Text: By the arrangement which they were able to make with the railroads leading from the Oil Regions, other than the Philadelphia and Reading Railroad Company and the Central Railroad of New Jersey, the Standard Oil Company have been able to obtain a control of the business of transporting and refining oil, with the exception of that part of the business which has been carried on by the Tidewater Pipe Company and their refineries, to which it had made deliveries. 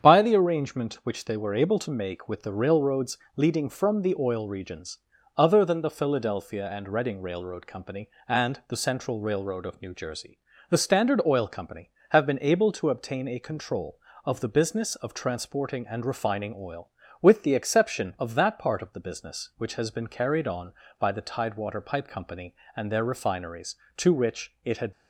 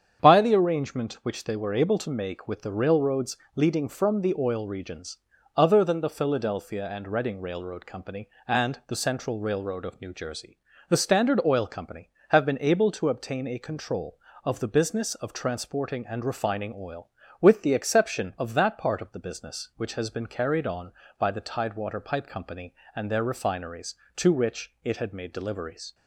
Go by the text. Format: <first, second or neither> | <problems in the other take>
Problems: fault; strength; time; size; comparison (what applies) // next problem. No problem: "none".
second | starts louder than the rest; strong; until 1.0 s; 8 dB; strong in the second // pauses between "railroads" and "leading"; slight; at 3.1 s; 0.16 s long; slight in the second // stops before "made deliveries"; at 24.9 s